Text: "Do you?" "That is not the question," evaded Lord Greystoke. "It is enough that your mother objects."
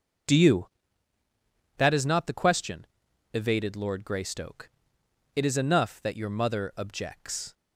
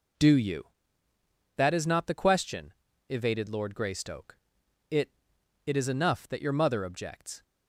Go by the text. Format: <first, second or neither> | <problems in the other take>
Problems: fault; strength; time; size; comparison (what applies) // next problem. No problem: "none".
first | says "It" twice; at 5.6 s